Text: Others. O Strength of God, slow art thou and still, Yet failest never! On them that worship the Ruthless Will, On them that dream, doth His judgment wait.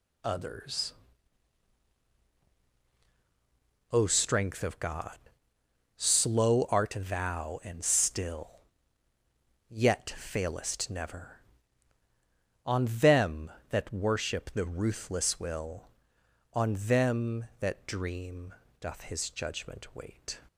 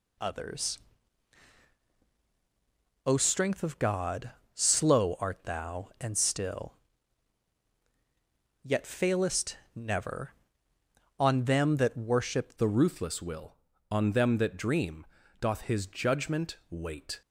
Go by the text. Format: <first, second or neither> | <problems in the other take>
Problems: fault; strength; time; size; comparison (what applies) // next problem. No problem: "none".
first | pauses between "failest" and "never"; slight; at 9.5 s; 0.18 s long // changes voice at "the"; from 12.5 s on; 4.7 s long